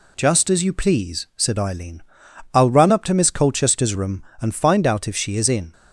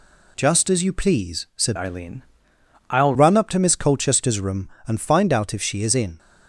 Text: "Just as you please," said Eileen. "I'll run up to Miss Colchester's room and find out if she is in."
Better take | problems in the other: first | changes voice from "Eileen" to "I'll"; from 1.7 to 3.1 s; 1.4 s long

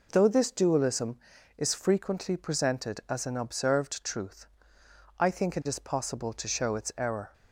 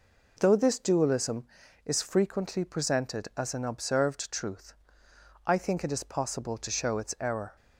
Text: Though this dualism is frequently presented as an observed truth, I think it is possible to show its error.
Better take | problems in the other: neither | none

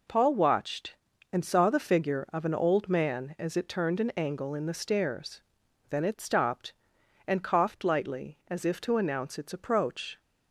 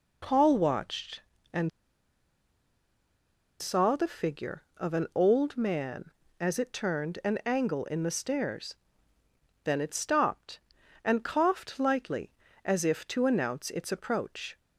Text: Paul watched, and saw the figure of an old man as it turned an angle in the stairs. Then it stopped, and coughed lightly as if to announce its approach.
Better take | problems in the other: first | pauses between "and" and "saw"; strong; at 1.6 s; 1.9 s long

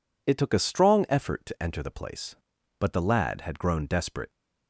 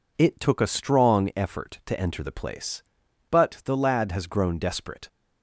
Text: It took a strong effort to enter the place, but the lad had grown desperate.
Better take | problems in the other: first | says "has" for "had"; at 4.1 s

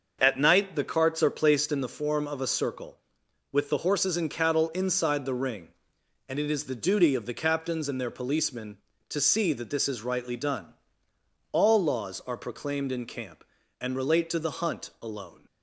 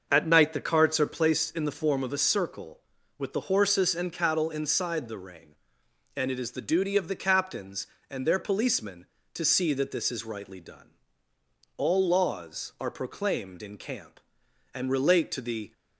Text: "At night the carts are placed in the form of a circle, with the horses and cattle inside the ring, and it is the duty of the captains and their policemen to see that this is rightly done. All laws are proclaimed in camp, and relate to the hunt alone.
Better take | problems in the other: first | starts louder than the rest; noticeable; until 1.1 s; 6 dB; also in the first // stops before "hunt alone"; at 15.7 s

